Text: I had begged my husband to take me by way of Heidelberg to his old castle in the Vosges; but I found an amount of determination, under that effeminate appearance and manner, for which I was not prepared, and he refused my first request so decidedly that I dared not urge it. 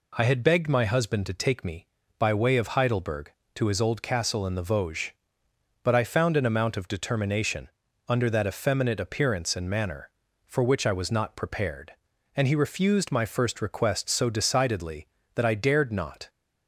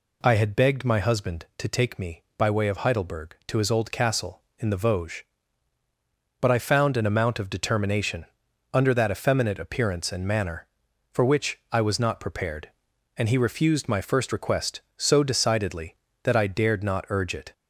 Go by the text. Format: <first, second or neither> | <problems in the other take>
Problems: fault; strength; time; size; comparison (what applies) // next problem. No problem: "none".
second | stops before "urge it"; at 16.2 s